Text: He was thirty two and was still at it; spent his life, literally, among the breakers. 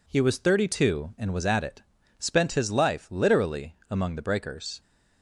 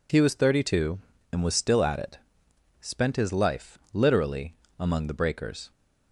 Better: second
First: skips "still"; at 1.4 s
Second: none

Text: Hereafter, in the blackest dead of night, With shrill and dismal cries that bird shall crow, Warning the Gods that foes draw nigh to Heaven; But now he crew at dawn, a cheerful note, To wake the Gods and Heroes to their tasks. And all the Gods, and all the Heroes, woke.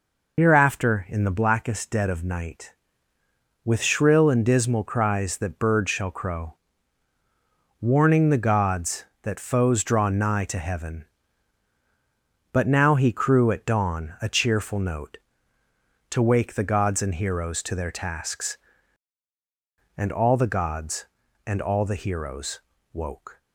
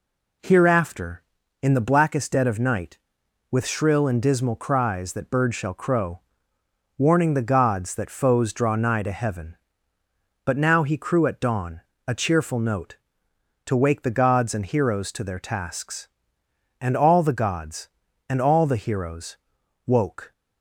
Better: second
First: loses the start of "Hereafter"; at 0.3 s; 60 ms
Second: none

